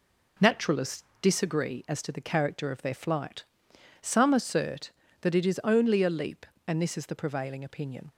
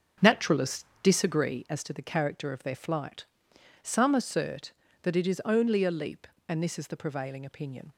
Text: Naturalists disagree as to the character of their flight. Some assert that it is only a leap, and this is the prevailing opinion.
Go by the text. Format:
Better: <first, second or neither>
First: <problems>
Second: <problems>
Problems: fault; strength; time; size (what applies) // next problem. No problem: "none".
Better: first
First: pauses between "Naturalists" and "disagree"; slight; at 1.0 s; 0.20 s long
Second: starts louder than the rest; strong; until 1.8 s; 7.5 dB // pauses between "Naturalists" and "disagree"; slight; at 0.8 s; 0.20 s long